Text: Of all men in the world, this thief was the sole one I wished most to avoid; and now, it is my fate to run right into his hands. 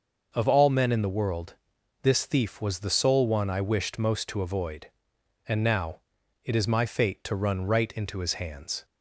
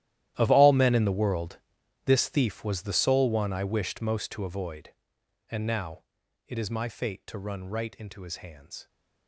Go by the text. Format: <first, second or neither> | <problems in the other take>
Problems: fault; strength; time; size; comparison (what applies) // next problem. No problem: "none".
first | gets quieter; strong; throughout; 18 dB // starts louder than the rest; strong; until 1.3 s; 13 dB; noticeable in the first